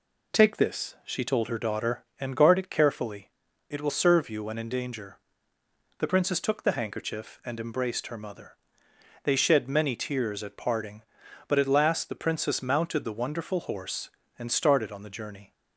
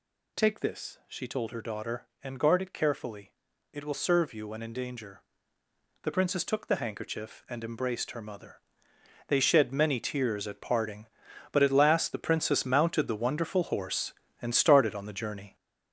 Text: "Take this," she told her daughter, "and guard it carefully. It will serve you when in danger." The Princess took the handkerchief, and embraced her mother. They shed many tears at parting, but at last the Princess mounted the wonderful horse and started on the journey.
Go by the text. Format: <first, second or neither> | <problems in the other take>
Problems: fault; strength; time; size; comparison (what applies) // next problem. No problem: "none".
first | gets louder; strong; throughout; 7 dB